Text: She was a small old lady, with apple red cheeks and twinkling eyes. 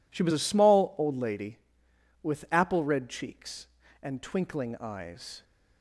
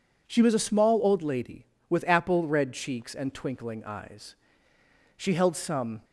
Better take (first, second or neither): first